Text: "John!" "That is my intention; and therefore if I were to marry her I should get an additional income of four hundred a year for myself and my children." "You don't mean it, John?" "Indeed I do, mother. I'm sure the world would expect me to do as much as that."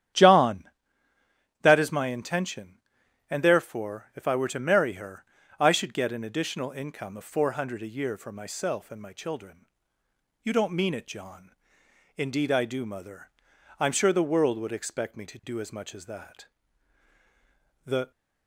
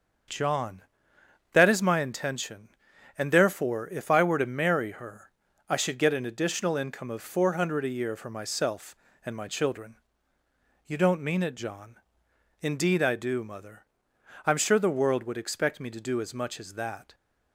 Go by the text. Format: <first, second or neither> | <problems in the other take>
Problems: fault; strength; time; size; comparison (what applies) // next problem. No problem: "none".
second | starts louder than the rest; strong; until 2.0 s; 10 dB; also in the second // pauses between "her" and "I"; slight; at 5.2 s; 0.36 s long; slight in the second // goes on to say "The"; slight; from 17.8 s on; 0.24 s long